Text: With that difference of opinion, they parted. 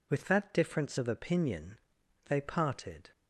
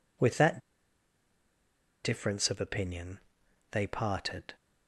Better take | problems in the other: first | pauses between "that" and "difference"; strong; at 0.5 s; 1.4 s long

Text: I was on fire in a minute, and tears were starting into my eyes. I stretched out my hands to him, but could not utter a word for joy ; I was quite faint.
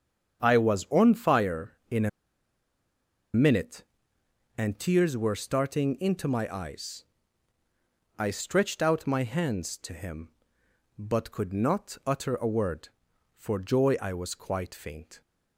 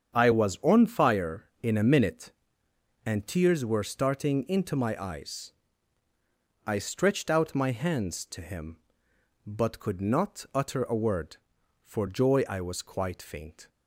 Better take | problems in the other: second | starts louder than the rest; strong; until 1.4 s; 7.5 dB; strong in the second // pauses between "a" and "minute"; strong; at 2.0 s; 1.2 s long

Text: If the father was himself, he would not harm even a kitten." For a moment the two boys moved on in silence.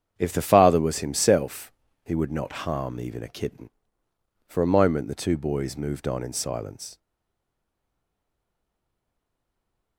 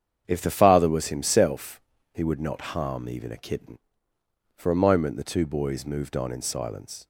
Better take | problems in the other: second | starts louder than the rest; strong; until 1.1 s; 8 dB; strong in the second // stays silent after the last word; strong; from 6.9 s on; 3.0 s long

